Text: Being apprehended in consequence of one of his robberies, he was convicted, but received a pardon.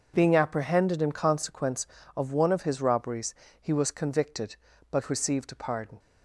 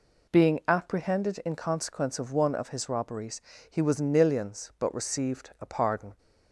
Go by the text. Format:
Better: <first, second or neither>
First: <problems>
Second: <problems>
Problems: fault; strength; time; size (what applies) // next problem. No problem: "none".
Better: first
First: none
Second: says "nillions" for "convicted"; at 4.0 s